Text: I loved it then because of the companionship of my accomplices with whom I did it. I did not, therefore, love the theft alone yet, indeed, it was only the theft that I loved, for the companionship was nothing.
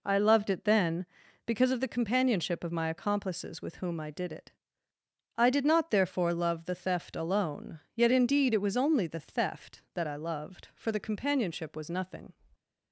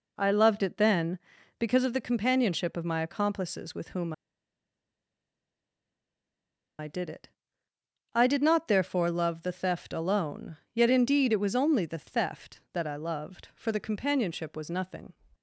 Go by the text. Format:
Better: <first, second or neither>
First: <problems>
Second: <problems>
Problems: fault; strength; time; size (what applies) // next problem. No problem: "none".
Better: first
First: pauses between "alone" and "yet"; slight; at 7.7 s; 0.16 s long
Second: pauses between "whom" and "I"; strong; at 4.1 s; 2.6 s long // pauses between "alone" and "yet"; slight; at 10.5 s; 0.18 s long